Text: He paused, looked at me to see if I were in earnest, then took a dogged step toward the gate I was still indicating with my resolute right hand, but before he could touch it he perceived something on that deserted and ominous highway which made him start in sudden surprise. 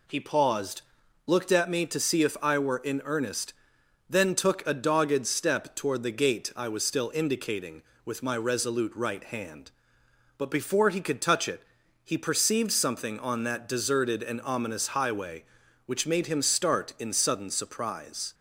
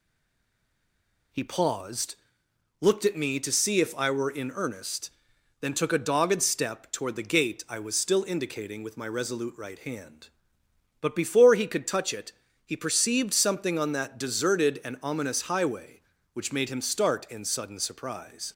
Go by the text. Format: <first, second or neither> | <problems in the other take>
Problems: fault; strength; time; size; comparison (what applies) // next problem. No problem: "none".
first | stays silent before the first word; noticeable; until 1.3 s; 1.3 s long // pauses between "it" and "he"; slight; at 12.3 s; 0.34 s long; also in the first